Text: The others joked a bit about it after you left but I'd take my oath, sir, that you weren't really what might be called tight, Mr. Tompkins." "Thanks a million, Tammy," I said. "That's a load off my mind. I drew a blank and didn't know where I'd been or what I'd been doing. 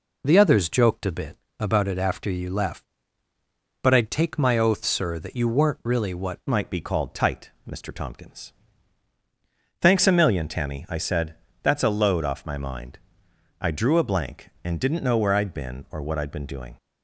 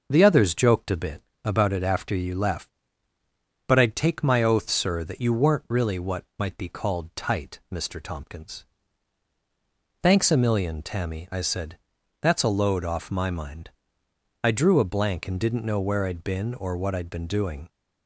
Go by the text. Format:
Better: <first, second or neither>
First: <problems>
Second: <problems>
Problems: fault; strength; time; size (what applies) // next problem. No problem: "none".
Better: second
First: pauses between "bit" and "about"; slight; at 1.3 s; 0.22 s long // changes voice at "might"; from 6.4 s on; 10.3 s long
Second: pauses between "bit" and "about"; slight; at 1.2 s; 0.22 s long